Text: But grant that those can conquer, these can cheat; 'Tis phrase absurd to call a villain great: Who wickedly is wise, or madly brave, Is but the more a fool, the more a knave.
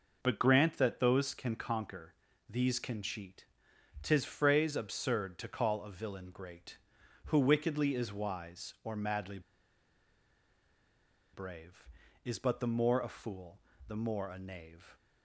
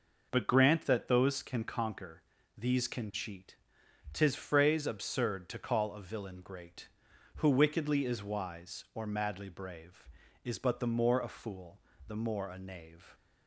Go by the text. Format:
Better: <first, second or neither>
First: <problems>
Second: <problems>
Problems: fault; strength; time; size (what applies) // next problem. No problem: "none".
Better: second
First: pauses between "madly" and "brave"; strong; at 9.4 s; 1.9 s long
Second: none